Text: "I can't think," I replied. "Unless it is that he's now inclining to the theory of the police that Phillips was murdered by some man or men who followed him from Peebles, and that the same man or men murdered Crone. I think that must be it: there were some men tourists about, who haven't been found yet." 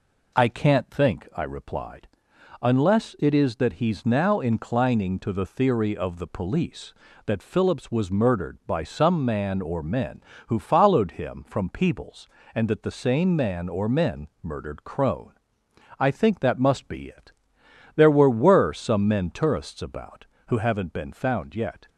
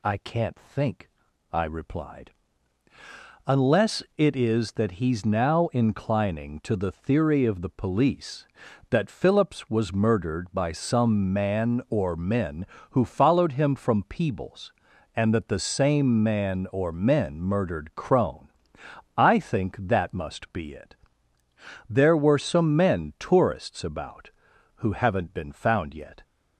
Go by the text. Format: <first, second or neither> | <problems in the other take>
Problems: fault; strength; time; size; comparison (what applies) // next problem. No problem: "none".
second | says "were" twice; at 18.3 s